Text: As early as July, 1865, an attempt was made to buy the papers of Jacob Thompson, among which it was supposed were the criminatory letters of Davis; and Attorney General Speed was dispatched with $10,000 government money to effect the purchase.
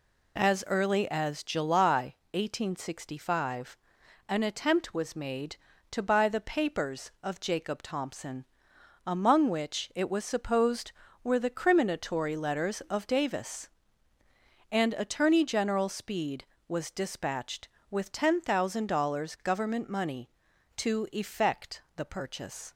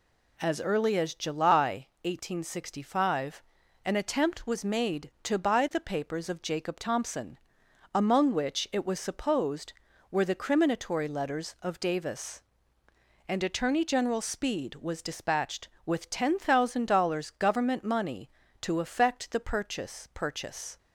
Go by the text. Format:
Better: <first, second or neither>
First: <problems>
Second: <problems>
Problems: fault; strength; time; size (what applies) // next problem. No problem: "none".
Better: first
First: none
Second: says "purchase" twice; at 20.1 s